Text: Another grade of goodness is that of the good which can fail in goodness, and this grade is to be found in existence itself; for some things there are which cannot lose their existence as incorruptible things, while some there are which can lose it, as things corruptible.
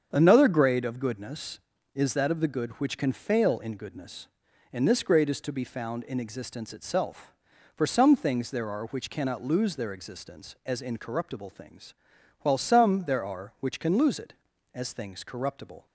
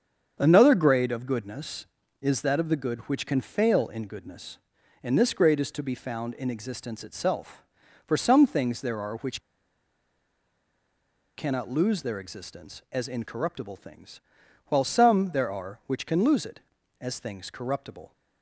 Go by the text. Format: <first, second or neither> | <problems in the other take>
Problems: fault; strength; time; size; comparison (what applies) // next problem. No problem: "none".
first | starts louder than the rest; strong; until 1.4 s; 7.5 dB; strong in the first // pauses between "which" and "cannot"; strong; at 9.4 s; 1.9 s long